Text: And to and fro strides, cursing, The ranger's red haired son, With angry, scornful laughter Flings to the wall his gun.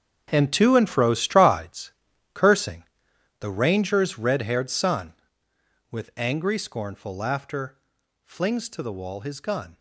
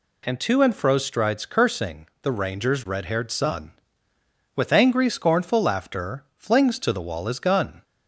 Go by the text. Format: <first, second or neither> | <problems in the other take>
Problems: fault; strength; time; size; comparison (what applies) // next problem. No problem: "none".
second | gets quieter; strong; throughout; 14 dB // pauses between "laughter" and "Flings"; at 7.7 s; 0.44 s long